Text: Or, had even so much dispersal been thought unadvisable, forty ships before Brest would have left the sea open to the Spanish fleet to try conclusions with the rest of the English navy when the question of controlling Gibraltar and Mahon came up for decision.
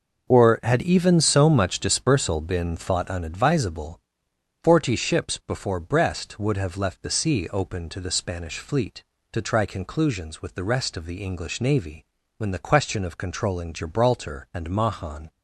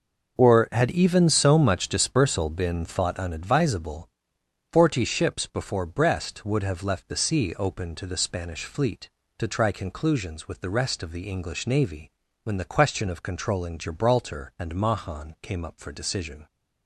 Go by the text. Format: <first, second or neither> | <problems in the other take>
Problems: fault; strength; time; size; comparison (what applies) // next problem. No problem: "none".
second | pauses between "navy" and "when"; slight; at 12.0 s; 0.32 s long; slight in the second // stops before "came up for decision"; at 15.2 s